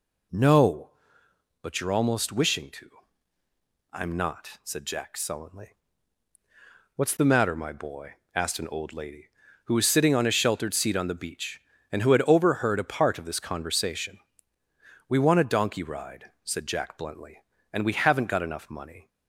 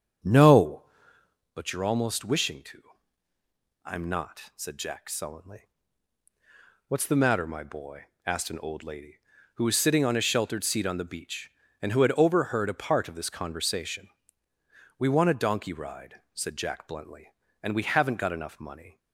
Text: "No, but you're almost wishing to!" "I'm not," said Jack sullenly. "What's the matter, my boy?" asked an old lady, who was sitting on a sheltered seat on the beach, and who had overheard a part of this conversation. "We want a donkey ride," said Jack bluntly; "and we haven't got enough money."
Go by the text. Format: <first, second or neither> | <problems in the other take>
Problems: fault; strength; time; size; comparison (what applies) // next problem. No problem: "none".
first | starts louder than the rest; strong; until 1.5 s; 7.5 dB